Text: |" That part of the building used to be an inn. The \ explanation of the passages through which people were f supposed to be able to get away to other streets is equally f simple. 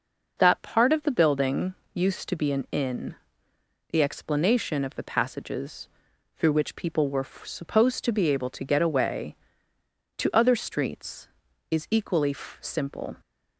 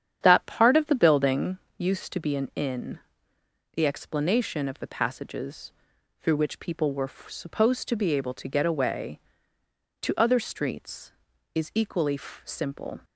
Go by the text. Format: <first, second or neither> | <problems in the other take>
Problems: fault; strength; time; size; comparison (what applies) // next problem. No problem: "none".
first | starts louder than the rest; strong; until 1.5 s; 9 dB // pauses between "building" and "used"; slight; at 1.5 s; 0.20 s long; slight in the first // pauses between "passages" and "through"; noticeable; at 5.7 s; 0.48 s long; noticeable in the first